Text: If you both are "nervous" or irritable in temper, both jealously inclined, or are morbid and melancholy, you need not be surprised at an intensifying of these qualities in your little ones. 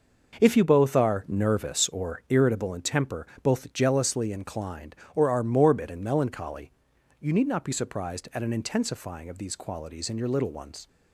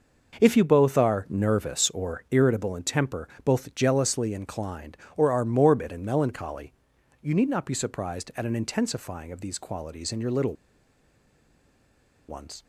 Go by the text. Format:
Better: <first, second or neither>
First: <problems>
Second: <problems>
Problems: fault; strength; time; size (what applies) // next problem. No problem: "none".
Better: first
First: none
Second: pauses between "little" and "ones"; strong; at 10.5 s; 1.7 s long